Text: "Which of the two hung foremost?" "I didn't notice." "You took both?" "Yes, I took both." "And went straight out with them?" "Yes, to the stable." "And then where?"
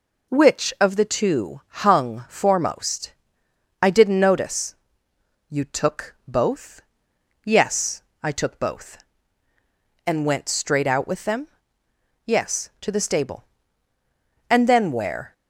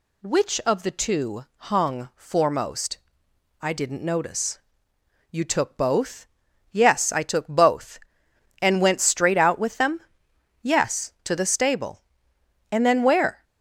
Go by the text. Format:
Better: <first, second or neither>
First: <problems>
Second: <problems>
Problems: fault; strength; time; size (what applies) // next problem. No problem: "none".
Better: neither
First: none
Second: none